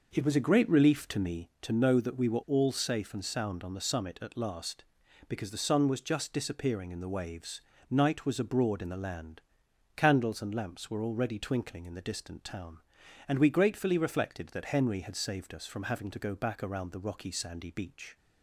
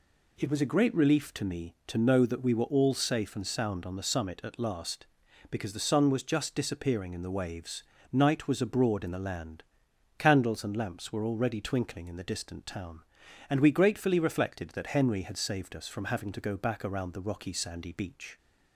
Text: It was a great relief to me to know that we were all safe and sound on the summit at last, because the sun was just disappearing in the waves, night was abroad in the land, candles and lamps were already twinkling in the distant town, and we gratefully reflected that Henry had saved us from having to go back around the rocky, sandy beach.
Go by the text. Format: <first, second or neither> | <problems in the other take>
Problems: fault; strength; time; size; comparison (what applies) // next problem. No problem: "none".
second | starts louder than the rest; noticeable; until 1.5 s; 5.5 dB